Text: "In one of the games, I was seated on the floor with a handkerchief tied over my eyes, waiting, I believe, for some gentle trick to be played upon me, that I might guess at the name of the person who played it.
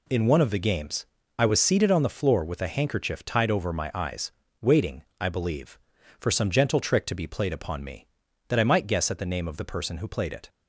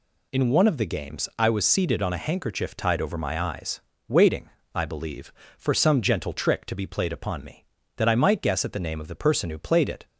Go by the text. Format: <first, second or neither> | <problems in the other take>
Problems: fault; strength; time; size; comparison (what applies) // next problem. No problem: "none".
first | skips "the floor with"; at 2.1 s